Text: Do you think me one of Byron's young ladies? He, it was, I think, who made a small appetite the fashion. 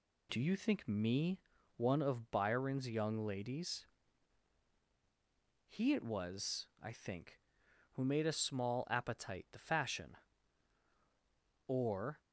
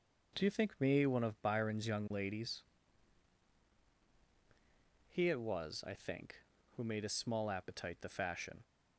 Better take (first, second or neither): second